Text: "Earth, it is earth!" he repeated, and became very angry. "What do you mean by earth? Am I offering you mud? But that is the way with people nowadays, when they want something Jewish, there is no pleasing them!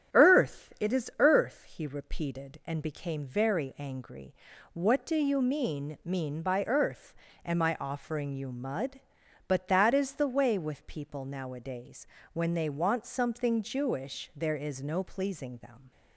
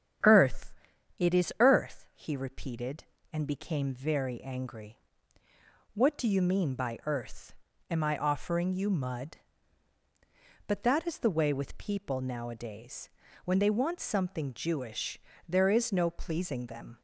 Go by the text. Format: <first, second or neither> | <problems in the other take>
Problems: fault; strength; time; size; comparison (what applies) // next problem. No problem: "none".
second | starts louder than the rest; strong; until 1.3 s; 9.5 dB; strong in the second // says "mean" twice; at 6.0 s